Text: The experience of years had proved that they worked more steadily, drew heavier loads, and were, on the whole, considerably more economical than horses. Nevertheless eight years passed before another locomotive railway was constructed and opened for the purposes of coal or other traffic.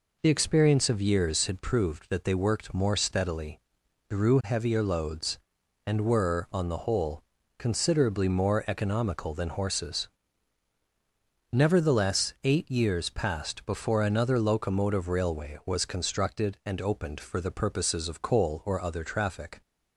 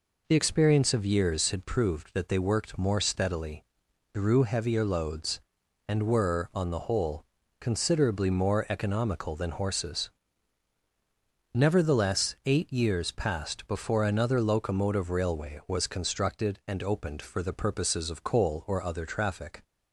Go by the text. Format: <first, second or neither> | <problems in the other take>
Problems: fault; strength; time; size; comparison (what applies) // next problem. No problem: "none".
neither | none